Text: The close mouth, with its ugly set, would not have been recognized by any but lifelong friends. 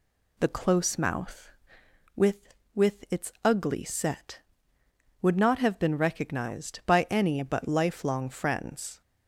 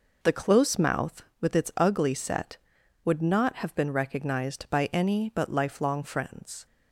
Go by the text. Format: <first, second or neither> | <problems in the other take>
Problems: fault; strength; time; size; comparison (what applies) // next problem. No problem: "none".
second | says "with" twice; at 2.7 s